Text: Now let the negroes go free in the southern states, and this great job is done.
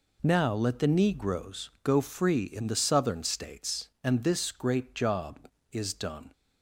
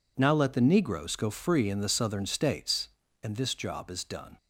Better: first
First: none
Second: skips "great"; at 3.5 s

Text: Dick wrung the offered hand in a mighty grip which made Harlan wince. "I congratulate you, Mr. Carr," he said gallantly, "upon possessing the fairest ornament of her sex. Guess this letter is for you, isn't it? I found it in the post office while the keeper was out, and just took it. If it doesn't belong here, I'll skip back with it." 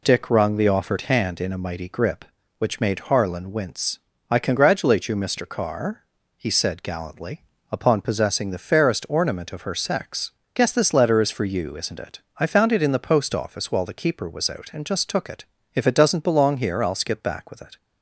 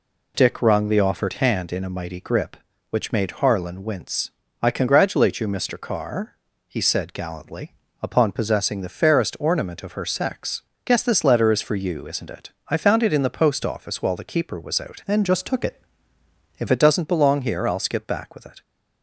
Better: first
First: none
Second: changes voice from "and" to "If"; from 15.0 to 16.6 s; 1.6 s long

